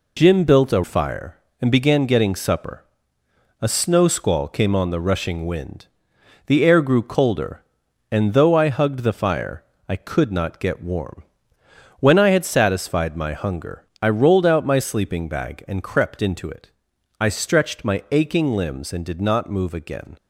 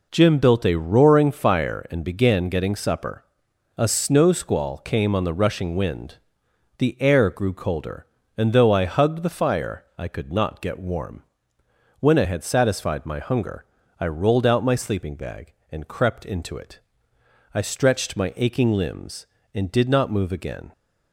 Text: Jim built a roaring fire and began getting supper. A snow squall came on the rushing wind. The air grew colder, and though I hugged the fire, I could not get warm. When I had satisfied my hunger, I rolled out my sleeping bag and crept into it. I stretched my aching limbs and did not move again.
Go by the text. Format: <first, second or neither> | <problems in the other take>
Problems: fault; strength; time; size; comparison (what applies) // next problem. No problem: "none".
second | skips "roaring"; at 0.8 s